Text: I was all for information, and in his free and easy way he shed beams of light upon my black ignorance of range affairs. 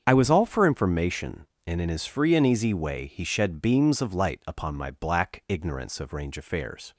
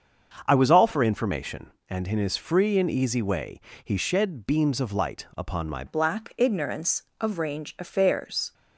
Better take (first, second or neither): first